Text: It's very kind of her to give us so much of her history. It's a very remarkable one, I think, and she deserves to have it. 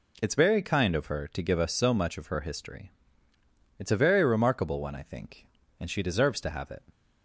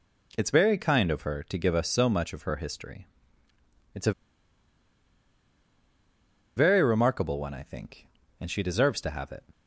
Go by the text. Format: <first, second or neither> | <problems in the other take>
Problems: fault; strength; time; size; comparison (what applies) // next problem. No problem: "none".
first | pauses between "a" and "very"; strong; at 4.1 s; 2.4 s long